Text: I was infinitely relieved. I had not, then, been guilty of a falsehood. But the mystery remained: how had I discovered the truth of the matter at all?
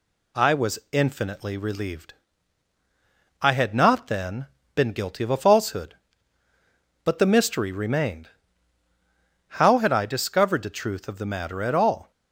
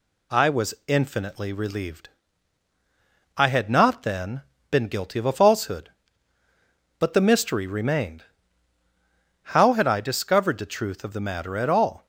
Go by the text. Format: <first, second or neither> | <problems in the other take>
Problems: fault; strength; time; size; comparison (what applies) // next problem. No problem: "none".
neither | none